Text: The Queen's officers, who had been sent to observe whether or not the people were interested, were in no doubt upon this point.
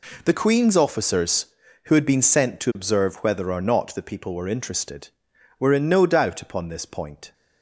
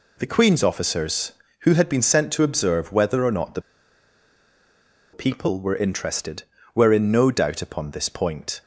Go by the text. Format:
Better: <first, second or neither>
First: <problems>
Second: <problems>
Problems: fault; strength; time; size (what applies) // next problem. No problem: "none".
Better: first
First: none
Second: pauses between "the" and "people"; strong; at 3.6 s; 1.5 s long